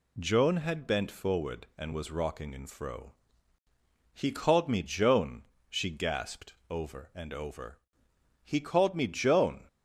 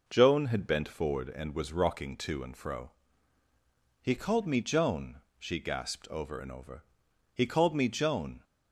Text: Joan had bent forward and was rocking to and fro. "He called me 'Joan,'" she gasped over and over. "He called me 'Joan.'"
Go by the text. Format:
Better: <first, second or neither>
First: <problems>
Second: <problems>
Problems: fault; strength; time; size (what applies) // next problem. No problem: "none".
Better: second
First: skips "to"; at 2.5 s // pauses between "gasped" and "over"; slight; at 6.5 s; 0.16 s long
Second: none